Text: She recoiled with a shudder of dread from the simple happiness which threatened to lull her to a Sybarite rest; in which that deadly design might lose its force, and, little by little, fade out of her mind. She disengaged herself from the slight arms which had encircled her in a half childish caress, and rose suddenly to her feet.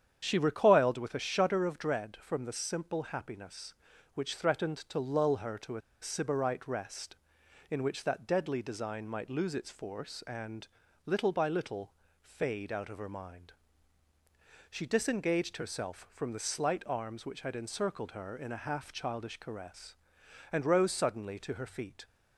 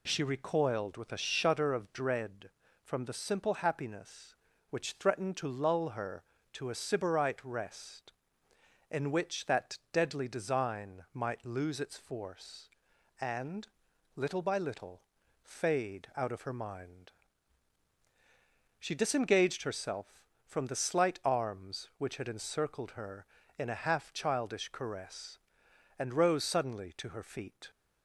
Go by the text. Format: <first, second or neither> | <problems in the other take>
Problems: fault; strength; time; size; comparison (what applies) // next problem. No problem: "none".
second | starts louder than the rest; strong; until 1.2 s; 8.5 dB // pauses between "a" and "Sybarite"; slight; at 5.8 s; 0.21 s long